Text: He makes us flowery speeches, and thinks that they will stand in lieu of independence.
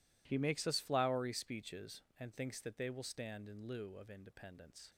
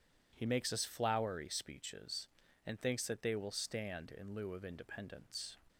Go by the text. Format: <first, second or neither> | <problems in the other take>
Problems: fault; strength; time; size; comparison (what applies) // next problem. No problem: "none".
neither | none